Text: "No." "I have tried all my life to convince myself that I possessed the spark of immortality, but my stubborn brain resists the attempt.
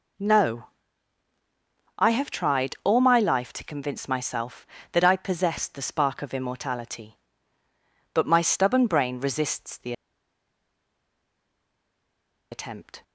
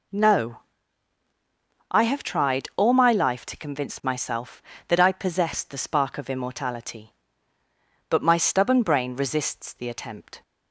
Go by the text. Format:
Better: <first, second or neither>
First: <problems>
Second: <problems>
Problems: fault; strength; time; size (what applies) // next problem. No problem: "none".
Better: second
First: pauses between "the" and "attempt"; strong; at 9.9 s; 2.5 s long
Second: none